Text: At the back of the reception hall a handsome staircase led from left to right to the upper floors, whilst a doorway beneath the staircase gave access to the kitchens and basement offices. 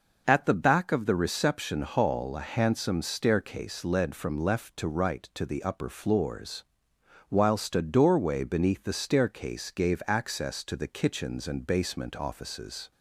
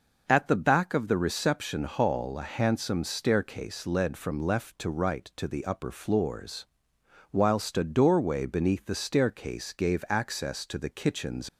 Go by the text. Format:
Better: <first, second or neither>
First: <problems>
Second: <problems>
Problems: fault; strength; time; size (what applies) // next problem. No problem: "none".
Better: first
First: none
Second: stops before "and basement offices"; at 11.4 s